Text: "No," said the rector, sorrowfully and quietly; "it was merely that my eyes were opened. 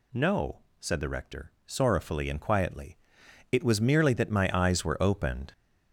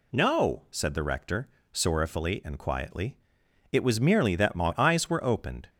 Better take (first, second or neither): second